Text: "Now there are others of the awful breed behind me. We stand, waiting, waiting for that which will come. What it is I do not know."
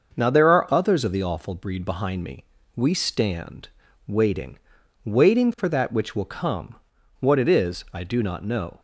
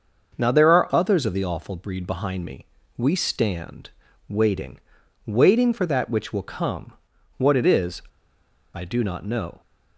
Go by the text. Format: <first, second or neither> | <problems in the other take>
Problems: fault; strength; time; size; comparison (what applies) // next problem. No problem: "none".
first | starts louder than the rest; until 1.3 s; 6.5 dB; also in the first // pauses between "is" and "I"; noticeable; at 8.0 s; 0.72 s long